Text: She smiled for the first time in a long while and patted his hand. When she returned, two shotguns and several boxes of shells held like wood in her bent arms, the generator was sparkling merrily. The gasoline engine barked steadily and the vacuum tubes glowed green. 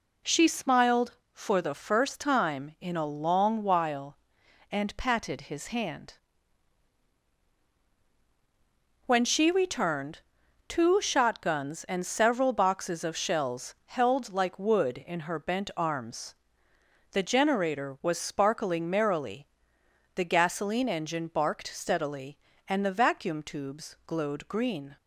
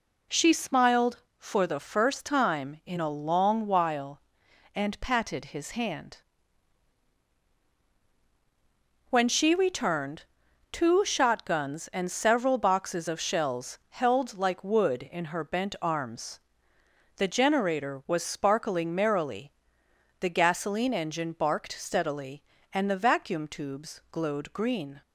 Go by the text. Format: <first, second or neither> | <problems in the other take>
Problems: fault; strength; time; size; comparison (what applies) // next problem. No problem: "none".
neither | none